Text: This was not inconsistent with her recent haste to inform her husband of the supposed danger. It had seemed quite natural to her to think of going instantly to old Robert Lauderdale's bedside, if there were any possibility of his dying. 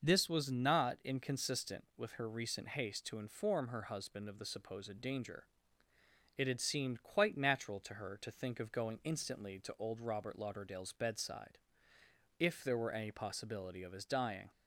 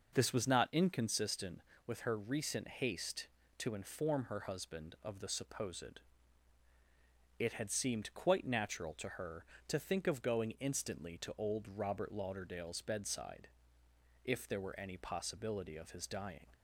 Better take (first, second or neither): first